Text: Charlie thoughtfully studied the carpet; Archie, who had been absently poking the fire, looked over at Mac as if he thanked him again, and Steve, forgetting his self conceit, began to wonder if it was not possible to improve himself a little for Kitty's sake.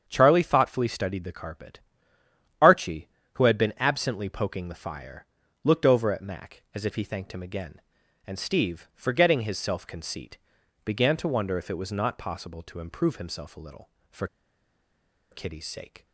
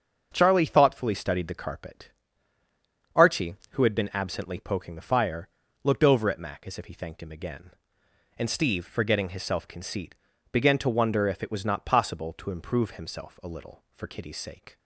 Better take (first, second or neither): second